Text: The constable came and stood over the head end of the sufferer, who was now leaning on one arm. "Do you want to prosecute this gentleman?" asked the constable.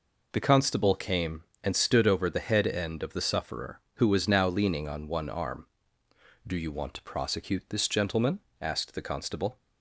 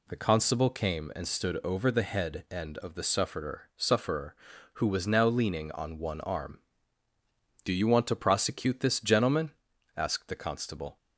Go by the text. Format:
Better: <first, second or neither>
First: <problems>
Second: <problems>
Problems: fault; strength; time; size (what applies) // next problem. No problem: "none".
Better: first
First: none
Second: says "sufferer" twice; at 3.7 s